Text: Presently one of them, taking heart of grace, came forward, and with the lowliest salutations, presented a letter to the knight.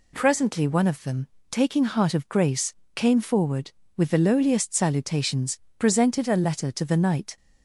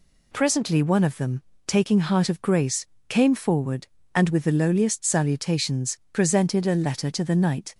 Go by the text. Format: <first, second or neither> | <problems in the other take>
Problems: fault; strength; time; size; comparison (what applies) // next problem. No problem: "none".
second | skips "and"; at 3.8 s